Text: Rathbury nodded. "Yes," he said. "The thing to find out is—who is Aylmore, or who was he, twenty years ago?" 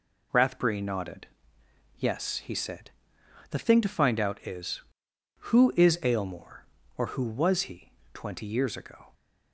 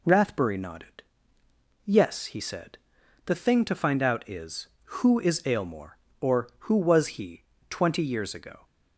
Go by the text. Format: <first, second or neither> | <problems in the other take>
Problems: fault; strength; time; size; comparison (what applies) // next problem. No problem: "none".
neither | none